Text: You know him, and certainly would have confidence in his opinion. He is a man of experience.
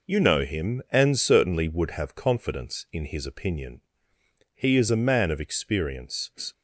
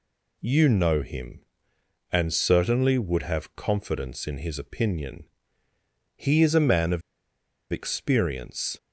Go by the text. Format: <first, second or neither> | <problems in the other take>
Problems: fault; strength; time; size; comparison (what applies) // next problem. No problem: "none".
first | pauses between "of" and "experience"; noticeable; at 7.0 s; 0.69 s long